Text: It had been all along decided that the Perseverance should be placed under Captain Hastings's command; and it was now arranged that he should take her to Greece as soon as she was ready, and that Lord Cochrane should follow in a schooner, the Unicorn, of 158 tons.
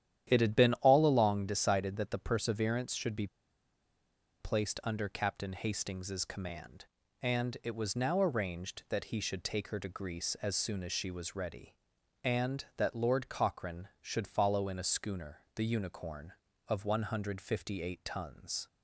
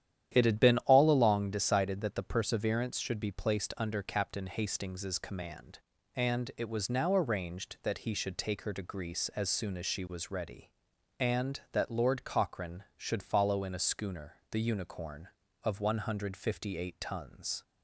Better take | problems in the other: second | starts louder than the rest; strong; until 1.2 s; 10.5 dB; strong in the second // pauses between "be" and "placed"; at 3.2 s; 1.1 s long

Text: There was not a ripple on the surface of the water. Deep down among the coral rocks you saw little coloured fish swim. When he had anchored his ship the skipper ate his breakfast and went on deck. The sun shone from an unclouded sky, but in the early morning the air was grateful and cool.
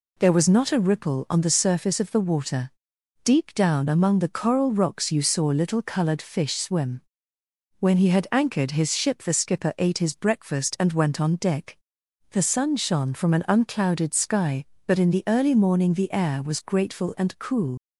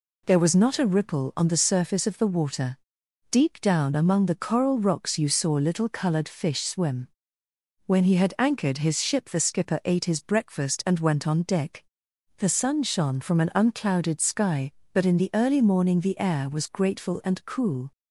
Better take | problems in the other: second | leaves "cool" unfinished; at 17.7 s; 70 ms

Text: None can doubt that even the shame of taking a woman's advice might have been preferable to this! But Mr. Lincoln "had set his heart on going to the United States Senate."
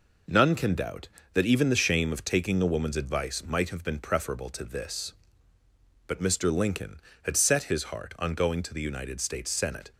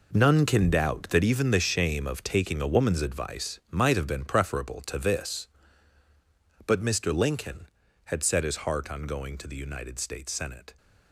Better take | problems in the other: first | gets quieter; strong; throughout; 12 dB

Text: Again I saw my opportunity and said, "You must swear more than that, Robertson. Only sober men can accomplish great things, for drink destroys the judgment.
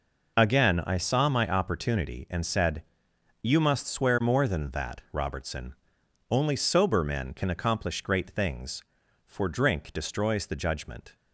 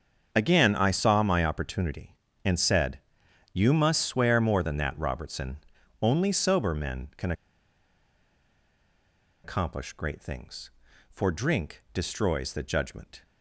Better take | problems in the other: first | starts louder than the rest; until 1.3 s; 7 dB // pauses between "can" and "accomplish"; strong; at 7.3 s; 2.1 s long

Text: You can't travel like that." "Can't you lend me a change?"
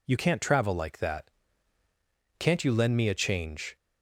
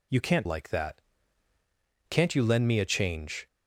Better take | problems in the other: first | skips "travel"; at 0.4 s

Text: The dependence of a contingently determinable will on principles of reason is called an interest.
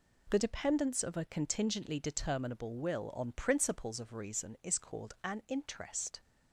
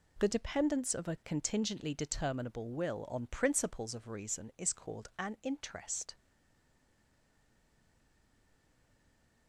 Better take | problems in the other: first | stays silent after the last word; strong; from 6.1 s on; 3.3 s long

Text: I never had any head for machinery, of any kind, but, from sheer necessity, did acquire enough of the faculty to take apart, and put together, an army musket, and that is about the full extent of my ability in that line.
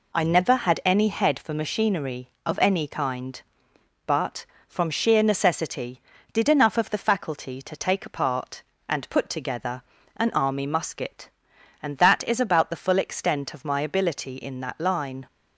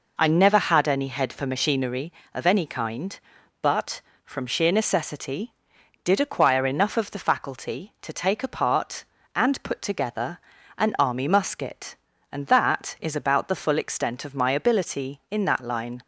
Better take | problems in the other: second | skips "acquire"; at 6.5 s

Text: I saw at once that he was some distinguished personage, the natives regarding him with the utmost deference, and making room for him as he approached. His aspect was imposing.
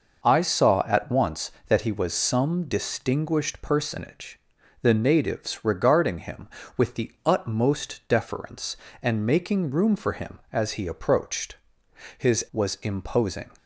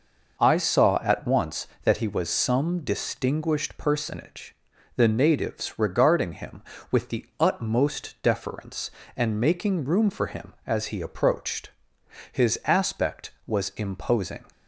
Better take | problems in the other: second | skips "aspect"; at 12.4 s

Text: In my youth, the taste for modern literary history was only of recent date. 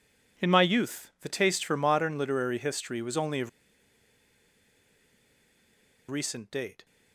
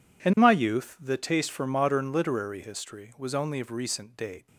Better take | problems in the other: second | pauses between "of" and "recent"; strong; at 3.4 s; 2.6 s long

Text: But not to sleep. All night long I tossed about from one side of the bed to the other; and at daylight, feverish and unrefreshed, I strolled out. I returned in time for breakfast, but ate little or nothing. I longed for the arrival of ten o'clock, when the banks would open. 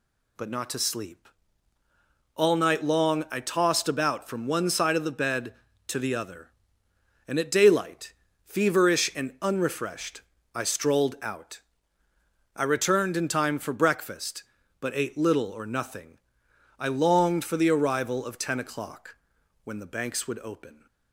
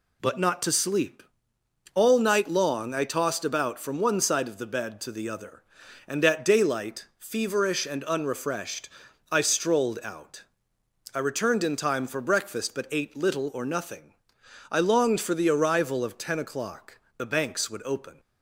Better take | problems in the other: first | skips "when"; at 17.0 s

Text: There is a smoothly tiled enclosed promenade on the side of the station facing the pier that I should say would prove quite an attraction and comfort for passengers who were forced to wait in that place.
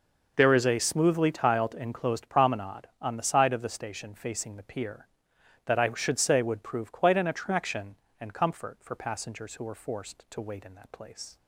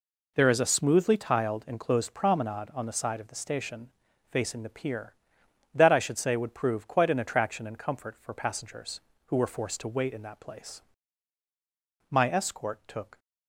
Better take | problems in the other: first | pauses between "station" and "facing"; at 3.8 s; 0.42 s long // goes on to say "My escort took"; noticeable; from 12.1 s on; 1.0 s long

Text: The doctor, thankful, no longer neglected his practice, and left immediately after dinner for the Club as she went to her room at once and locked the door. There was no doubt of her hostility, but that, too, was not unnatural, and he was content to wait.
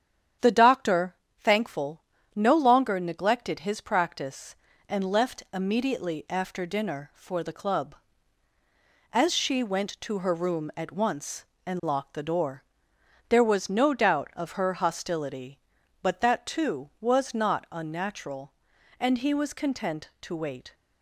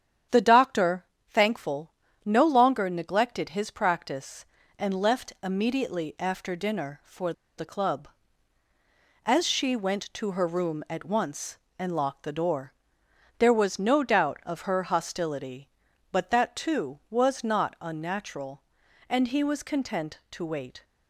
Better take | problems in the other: first | starts louder than the rest; strong; until 1.5 s; 9 dB; strong in the first // pauses between "for" and "the"; slight; at 7.3 s; 0.25 s long

